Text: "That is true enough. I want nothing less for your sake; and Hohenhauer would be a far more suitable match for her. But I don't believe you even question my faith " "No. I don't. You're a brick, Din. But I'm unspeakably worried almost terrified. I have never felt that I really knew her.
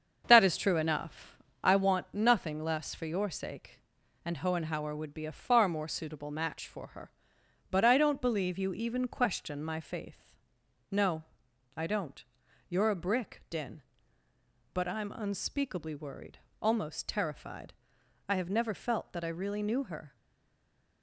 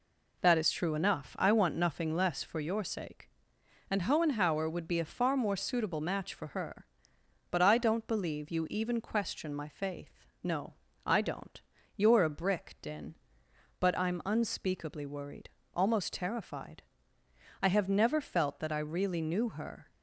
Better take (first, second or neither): second